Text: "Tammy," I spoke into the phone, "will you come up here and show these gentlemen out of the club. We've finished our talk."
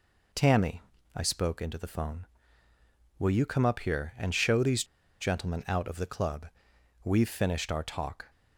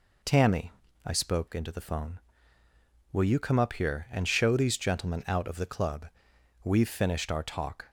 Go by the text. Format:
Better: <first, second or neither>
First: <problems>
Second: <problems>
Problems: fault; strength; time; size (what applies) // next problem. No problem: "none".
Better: second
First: pauses between "these" and "gentlemen"; at 4.8 s; 0.36 s long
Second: none